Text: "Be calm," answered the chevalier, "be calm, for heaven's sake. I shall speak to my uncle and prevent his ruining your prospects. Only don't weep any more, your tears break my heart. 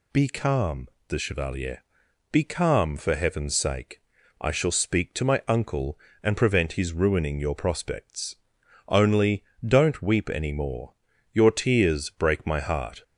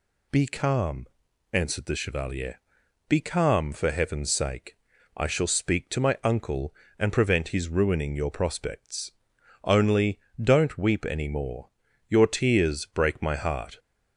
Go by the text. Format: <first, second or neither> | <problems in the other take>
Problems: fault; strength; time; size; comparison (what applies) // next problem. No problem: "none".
second | skips "answered"; at 0.9 s // pauses between "Only" and "don't"; slight; at 9.4 s; 0.24 s long; slight in the second